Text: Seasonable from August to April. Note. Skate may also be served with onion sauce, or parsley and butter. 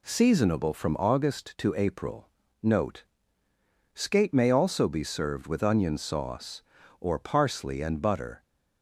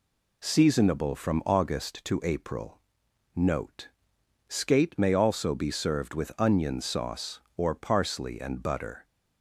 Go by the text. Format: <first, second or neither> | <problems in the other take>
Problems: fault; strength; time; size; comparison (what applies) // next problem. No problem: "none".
neither | none